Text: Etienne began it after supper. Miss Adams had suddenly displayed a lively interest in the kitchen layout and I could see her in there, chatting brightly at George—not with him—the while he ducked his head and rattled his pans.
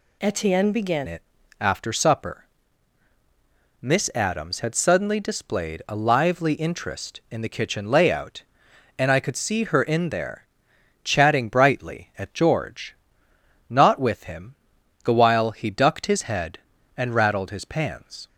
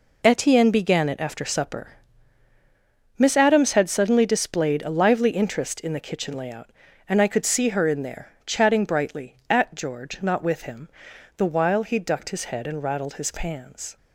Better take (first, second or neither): second